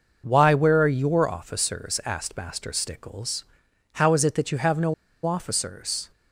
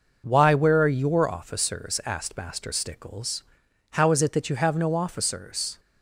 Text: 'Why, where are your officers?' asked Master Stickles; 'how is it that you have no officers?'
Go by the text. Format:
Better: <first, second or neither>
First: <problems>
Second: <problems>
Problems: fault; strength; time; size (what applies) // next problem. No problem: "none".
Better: second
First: pauses between "no" and "officers"; slight; at 4.9 s; 0.31 s long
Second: none